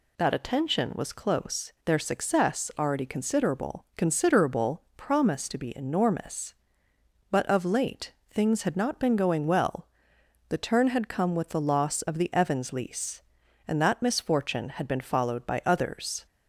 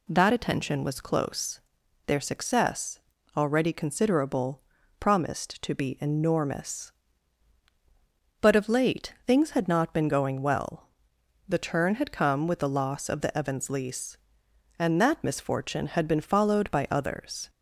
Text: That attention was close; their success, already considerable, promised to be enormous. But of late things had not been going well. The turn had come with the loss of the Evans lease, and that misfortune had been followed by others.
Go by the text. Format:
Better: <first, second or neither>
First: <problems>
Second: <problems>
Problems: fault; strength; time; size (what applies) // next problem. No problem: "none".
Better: second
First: says "considerable" twice; at 3.9 s // pauses between "late" and "things"; slight; at 8.1 s; 0.16 s long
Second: none